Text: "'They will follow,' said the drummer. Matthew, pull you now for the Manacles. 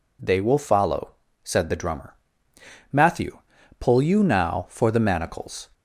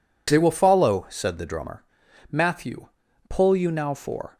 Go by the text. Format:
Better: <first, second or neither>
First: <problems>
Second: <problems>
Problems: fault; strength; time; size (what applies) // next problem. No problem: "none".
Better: first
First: none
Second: stops before "the Manacles"; at 4.3 s